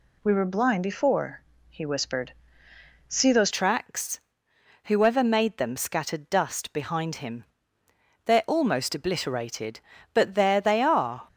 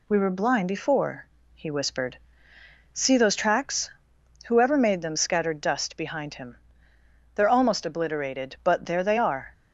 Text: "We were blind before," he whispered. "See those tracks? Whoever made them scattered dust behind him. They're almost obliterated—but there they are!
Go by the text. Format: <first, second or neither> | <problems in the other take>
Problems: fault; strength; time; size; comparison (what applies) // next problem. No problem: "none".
second | changes voice at "tracks"; from 3.5 s on; 7.7 s long